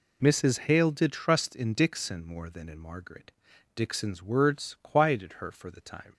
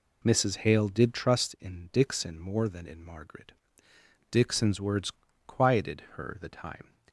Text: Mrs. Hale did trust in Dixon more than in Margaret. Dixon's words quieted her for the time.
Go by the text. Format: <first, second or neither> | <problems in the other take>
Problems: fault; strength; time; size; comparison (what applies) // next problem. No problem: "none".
first | pauses between "words" and "quieted"; slight; at 5.1 s; 0.36 s long // skips "for"; at 6.3 s